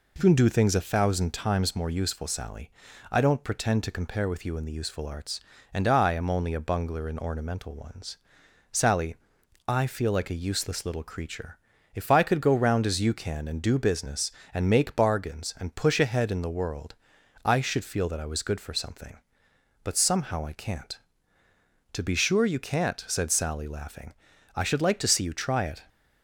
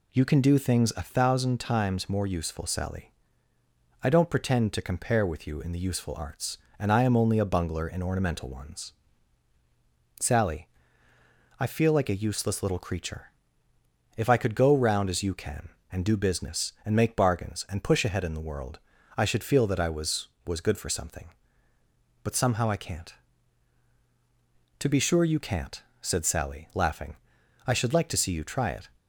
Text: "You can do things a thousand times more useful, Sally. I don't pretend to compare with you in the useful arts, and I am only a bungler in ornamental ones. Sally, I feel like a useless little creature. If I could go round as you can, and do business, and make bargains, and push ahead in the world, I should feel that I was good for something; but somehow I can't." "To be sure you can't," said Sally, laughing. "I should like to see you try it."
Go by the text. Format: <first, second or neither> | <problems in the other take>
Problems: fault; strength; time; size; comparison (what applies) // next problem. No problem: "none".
first | says "was" twice; at 20.4 s